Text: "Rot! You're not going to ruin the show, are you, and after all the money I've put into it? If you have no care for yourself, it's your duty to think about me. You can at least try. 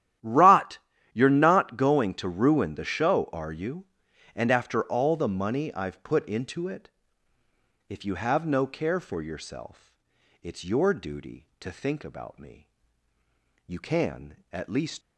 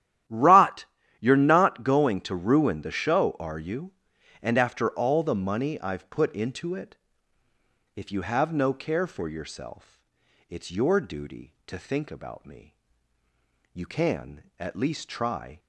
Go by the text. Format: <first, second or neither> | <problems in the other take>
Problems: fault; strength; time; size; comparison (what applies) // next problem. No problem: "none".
second | starts louder than the rest; strong; until 1.5 s; 11.5 dB; strong in the second // stops before "try"; at 15.0 s